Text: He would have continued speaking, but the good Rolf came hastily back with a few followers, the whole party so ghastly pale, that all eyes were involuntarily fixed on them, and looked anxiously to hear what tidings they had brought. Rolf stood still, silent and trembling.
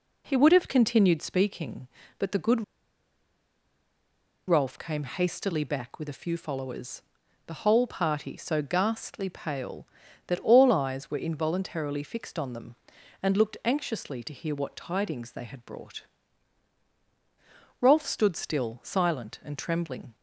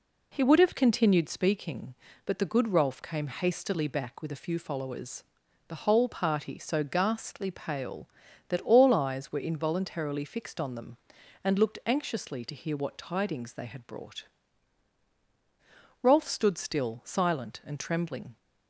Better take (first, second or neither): second